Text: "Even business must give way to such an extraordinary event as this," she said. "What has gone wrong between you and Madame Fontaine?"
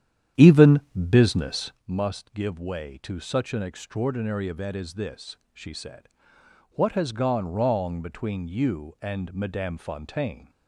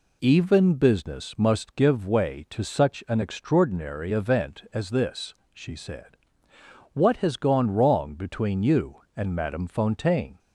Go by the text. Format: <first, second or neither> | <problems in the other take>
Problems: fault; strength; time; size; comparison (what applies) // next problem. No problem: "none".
second | starts louder than the rest; strong; until 1.8 s; 10 dB // pauses between "Even" and "business"; slight; at 0.7 s; 0.30 s long